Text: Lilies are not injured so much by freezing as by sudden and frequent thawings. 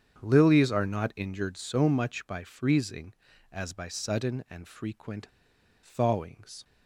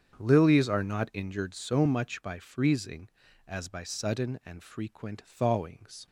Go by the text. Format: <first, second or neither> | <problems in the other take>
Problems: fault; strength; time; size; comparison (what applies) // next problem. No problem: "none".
second | starts louder than the rest; strong; until 1.2 s; 8 dB; strong in the second // pauses between "frequent" and "thawings"; noticeable; at 5.2 s; 0.57 s long